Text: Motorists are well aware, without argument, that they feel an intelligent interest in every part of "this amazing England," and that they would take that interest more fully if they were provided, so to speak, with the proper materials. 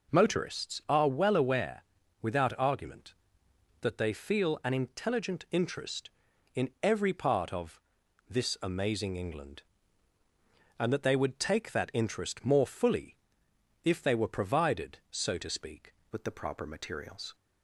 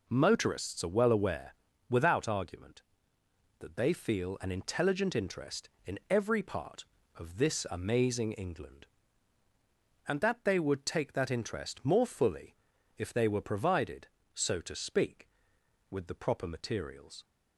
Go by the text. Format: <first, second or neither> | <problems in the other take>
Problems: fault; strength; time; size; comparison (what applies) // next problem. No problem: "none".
second | pauses between "of" and "this"; noticeable; at 7.7 s; 0.48 s long // pauses between "fully" and "if"; noticeable; at 13.1 s; 0.68 s long; also in the second // changes voice at "with"; from 16.1 s on; 1.2 s long